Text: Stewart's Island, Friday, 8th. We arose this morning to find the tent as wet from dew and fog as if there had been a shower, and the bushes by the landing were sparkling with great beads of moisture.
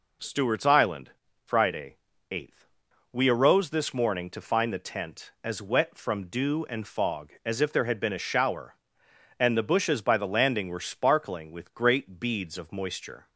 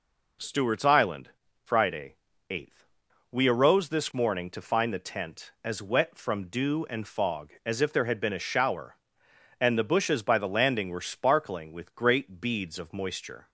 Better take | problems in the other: neither | none

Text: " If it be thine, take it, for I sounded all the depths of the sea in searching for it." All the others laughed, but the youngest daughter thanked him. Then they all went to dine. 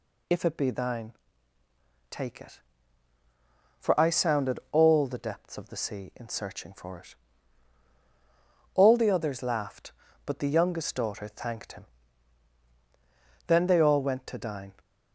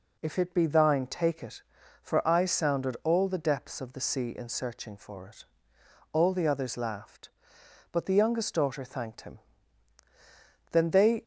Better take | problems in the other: first | stops before "all went to dine"; at 11.2 s

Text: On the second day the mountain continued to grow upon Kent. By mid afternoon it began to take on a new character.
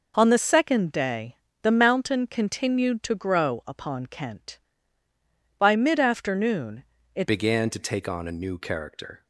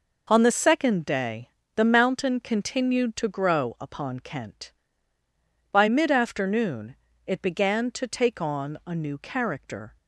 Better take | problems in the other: second | pauses between "day" and "the"; slight; at 1.3 s; 0.28 s long; slight in the second // pauses between "afternoon" and "it"; slight; at 6.8 s; 0.30 s long; slight in the second // changes voice at "began"; from 7.2 s on; 2.0 s long

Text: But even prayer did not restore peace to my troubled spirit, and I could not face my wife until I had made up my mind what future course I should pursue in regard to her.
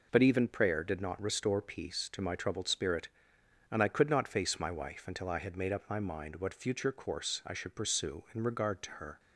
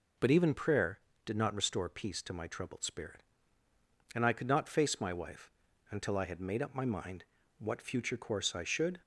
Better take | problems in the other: first | pauses between "wife" and "until"; at 5.5 s; 0.38 s long // pauses between "mind" and "what"; slight; at 7.2 s; 0.36 s long // stops before "pursue in regard to her"; at 9.0 s

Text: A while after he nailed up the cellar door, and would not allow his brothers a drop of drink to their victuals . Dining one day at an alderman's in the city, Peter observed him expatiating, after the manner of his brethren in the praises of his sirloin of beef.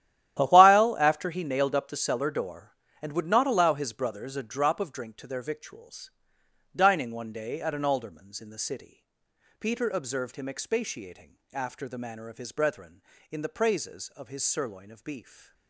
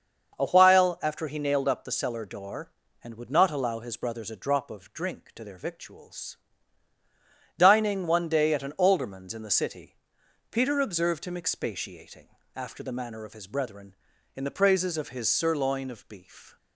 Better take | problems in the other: second | gets quieter; strong; throughout; 14 dB // starts louder than the rest; strong; until 1.4 s; 12 dB; also in the second

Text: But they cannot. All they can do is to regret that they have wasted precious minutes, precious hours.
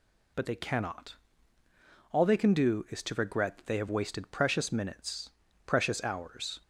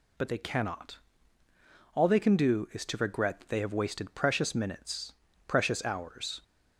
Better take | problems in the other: neither | none

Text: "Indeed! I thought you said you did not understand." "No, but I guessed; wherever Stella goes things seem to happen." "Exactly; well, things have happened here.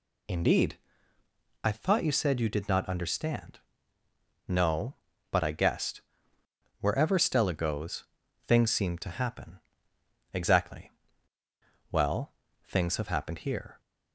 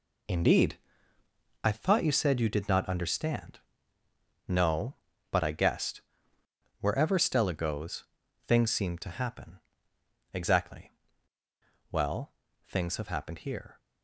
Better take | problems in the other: first | gets quieter; strong; throughout; 10 dB // pauses between "goes" and "things"; at 8.0 s; 0.42 s long; also in the first

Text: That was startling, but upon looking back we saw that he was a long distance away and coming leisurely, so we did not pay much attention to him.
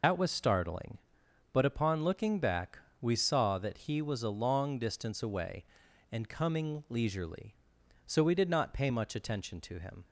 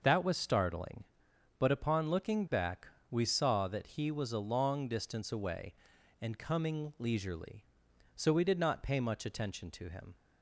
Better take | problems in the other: second | loses the start of "That"; at 0.0 s; 65 ms // pauses between "back" and "we"; slight; at 2.7 s; 0.20 s long; slight in the second

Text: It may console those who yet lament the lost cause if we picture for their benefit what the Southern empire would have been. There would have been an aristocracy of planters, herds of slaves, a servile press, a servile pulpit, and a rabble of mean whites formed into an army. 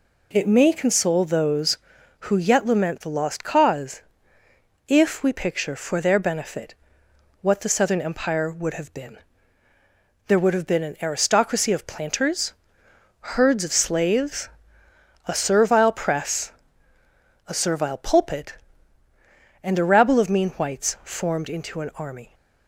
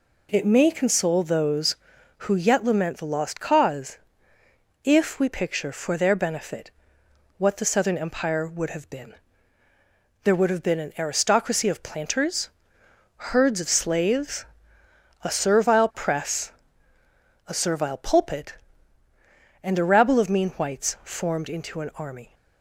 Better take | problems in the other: neither | pauses between "cause" and "if"; noticeable; the same in both // pauses between "benefit" and "what"; noticeable; the same in both

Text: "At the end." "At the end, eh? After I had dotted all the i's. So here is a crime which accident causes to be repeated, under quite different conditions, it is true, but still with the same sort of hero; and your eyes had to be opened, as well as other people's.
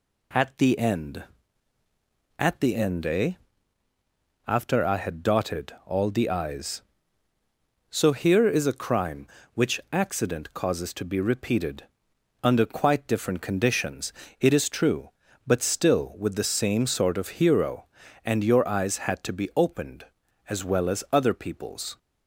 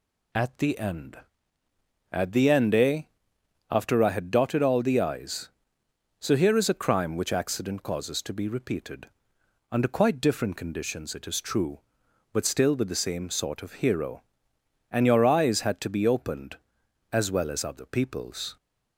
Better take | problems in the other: neither | none

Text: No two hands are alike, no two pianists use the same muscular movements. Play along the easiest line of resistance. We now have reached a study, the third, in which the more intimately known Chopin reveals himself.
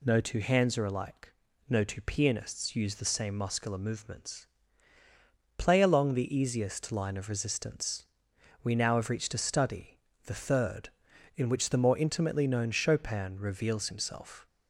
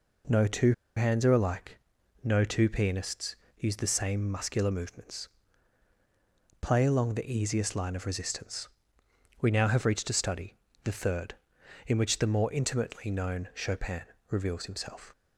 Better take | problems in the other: first | pauses between "two" and "hands"; slight; at 0.7 s; 0.24 s long // pauses between "pianists" and "use"; slight; at 3.3 s; 0.24 s long // pauses between "Chopin" and "reveals"; slight; at 14.0 s; 0.26 s long

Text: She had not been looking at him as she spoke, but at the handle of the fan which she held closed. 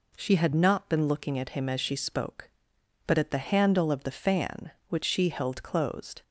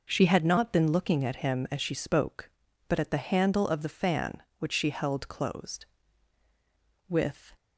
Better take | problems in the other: first | goes on to say "With"; slight; from 7.0 s on; 0.44 s long

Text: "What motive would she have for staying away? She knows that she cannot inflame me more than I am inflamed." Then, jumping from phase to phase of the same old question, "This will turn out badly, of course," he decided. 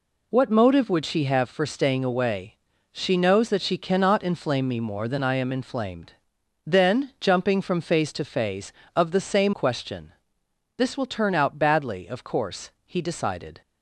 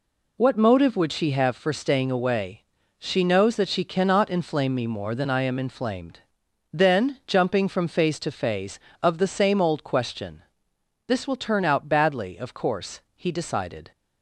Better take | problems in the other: second | skips "old"; at 9.5 s

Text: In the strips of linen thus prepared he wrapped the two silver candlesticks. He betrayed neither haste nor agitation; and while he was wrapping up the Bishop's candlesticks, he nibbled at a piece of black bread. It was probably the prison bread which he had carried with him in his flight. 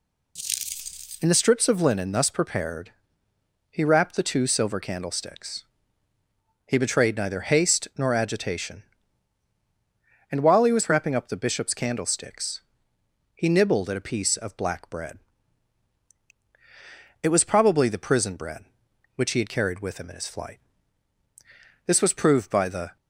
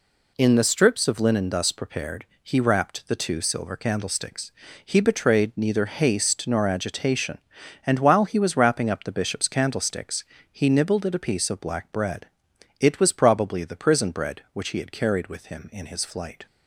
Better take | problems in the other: second | pauses between "prepared" and "he"; noticeable; at 2.9 s; 0.78 s long; slight in the second // goes on to say "This was proved by the"; noticeable; from 21.8 s on; 1.1 s long

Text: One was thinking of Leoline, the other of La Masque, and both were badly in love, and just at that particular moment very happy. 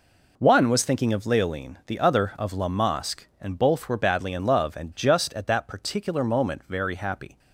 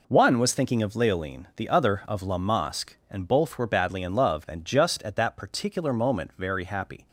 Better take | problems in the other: neither | none

